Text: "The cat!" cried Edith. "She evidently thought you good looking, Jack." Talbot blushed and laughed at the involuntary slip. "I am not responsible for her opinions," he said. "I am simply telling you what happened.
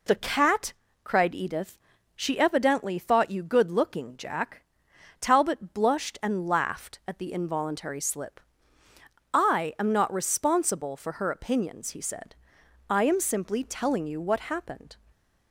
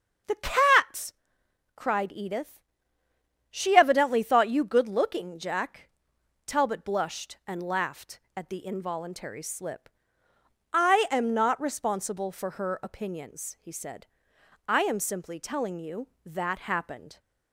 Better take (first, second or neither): first